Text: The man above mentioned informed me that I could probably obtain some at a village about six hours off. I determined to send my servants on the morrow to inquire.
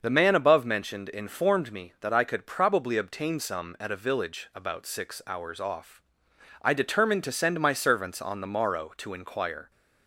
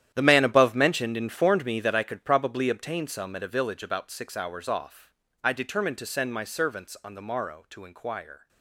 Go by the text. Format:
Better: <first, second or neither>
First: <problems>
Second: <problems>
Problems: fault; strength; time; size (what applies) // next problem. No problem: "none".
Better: first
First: starts louder than the rest; until 1.0 s; 6.5 dB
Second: gets quieter; strong; throughout; 14 dB // starts louder than the rest; strong; until 1.1 s; 11 dB